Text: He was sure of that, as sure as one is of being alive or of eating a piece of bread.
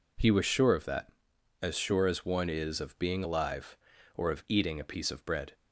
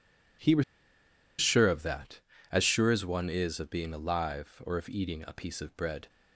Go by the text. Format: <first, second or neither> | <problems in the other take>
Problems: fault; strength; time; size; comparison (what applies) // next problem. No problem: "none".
first | pauses between "was" and "sure"; noticeable; at 0.6 s; 0.76 s long